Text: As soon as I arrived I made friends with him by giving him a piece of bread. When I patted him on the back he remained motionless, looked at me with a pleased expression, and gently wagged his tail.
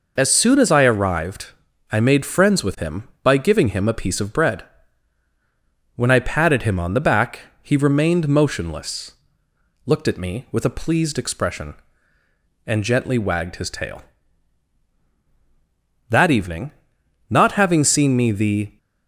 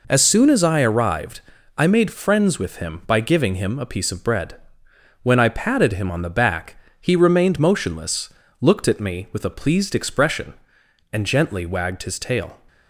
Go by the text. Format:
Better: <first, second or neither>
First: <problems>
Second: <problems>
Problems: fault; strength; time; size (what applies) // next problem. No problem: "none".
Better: second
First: pauses between "arrived" and "I"; at 1.4 s; 0.44 s long // pauses between "back" and "he"; slight; at 7.4 s; 0.20 s long // goes on to say "That evening not having seen me the"; strong; from 16.0 s on; 2.6 s long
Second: pauses between "arrived" and "I"; at 1.3 s; 0.38 s long // pauses between "back" and "he"; slight; at 6.7 s; 0.24 s long